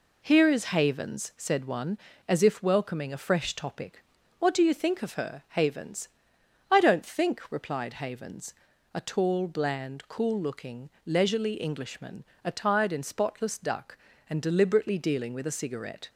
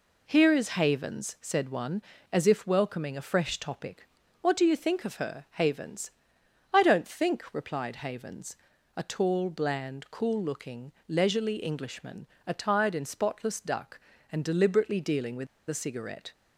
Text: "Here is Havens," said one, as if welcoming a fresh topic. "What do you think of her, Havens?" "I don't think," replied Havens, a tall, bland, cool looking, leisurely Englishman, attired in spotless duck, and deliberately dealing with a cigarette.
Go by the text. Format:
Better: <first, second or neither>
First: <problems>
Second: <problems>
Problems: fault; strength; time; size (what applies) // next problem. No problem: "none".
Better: first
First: none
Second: pauses between "with" and "a"; slight; at 15.4 s; 0.20 s long